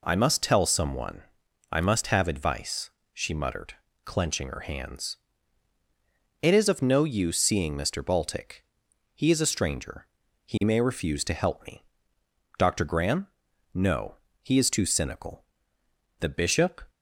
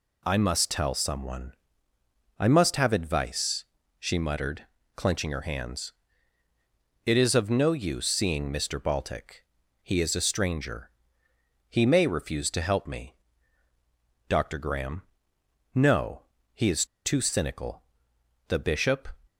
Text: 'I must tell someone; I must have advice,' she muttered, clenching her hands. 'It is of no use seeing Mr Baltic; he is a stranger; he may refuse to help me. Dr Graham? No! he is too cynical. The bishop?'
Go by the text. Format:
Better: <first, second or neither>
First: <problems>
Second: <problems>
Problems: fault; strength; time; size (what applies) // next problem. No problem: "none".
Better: first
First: none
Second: pauses between "is" and "too"; slight; at 16.8 s; 0.20 s long